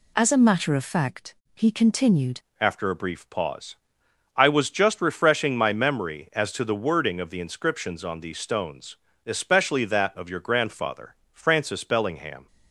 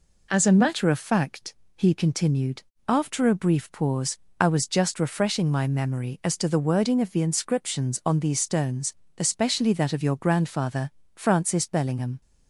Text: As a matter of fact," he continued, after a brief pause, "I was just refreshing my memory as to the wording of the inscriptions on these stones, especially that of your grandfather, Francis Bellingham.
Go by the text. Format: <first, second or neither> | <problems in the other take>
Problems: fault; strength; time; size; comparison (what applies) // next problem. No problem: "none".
second | changes voice at "after"; from 2.5 s on; 9.9 s long